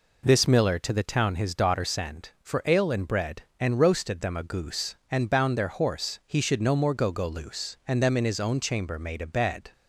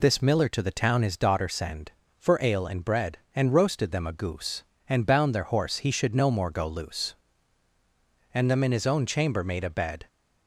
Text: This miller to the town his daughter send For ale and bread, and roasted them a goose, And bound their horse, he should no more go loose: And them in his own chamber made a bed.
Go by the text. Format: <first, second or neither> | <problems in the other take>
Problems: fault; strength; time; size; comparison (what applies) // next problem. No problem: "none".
second | says "go" twice; at 7.1 s